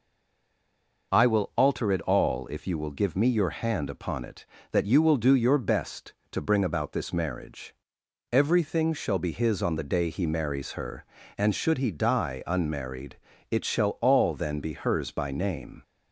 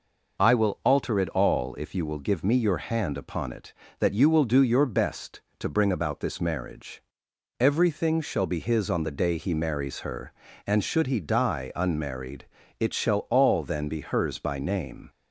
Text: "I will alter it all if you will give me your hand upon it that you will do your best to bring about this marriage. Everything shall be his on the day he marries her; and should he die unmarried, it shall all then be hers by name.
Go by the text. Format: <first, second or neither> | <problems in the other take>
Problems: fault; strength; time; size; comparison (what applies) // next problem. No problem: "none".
second | stays silent before the first word; until 1.1 s; 1.1 s long